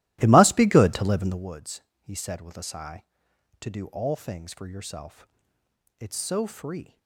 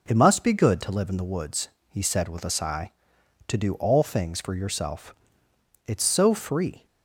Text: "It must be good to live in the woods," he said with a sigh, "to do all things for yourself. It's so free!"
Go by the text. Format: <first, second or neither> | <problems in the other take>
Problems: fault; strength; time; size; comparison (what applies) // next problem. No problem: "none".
second | starts louder than the rest; strong; until 1.6 s; 15.5 dB